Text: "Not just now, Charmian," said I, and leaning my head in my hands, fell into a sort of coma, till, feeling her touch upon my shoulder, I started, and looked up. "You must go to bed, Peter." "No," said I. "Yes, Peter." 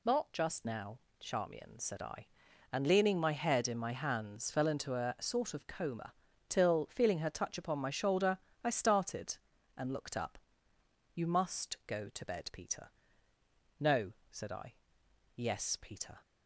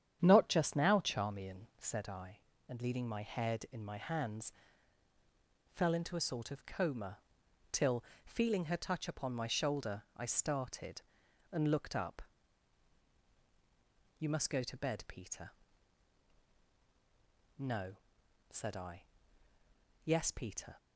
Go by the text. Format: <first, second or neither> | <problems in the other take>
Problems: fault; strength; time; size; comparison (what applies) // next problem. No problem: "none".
first | starts louder than the rest; strong; until 2.0 s; 9 dB